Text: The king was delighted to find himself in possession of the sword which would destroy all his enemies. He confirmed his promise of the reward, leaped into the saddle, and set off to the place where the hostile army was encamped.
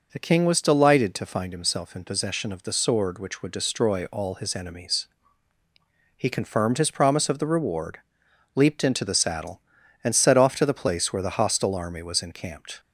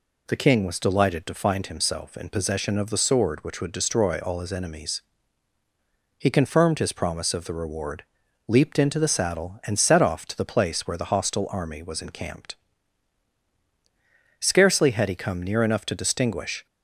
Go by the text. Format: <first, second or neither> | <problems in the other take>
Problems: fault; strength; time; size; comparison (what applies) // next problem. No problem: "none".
first | goes on to say "Scarcely had he come near enough to distinguish"; strong; from 14.3 s on; 2.2 s long